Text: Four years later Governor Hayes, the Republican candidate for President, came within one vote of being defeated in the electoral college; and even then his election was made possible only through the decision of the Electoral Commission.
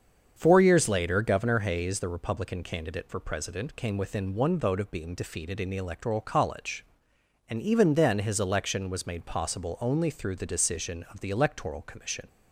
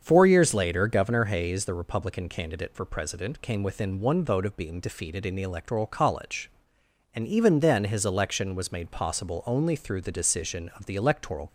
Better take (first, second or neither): first